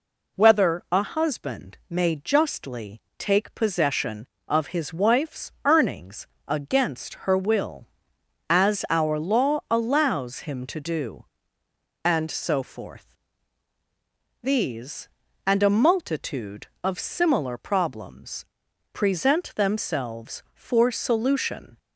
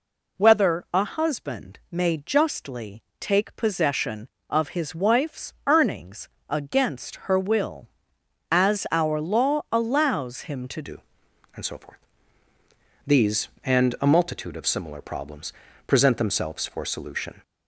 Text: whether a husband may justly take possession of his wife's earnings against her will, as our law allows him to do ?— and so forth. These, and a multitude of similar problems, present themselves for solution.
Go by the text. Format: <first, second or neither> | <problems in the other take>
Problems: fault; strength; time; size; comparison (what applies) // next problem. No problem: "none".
first | pauses between "justly" and "take"; slight; at 3.0 s; 0.18 s long; slight in the first // pauses between "earnings" and "against"; slight; at 6.2 s; 0.20 s long; slight in the first // changes voice at "do"; from 10.8 s on; 6.6 s long